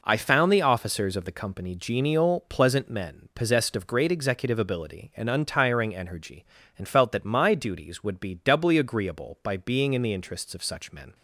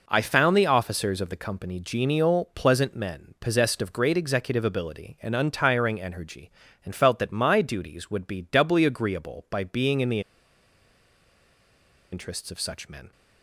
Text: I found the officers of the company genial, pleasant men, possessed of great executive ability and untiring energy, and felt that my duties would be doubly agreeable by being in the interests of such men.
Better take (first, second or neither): first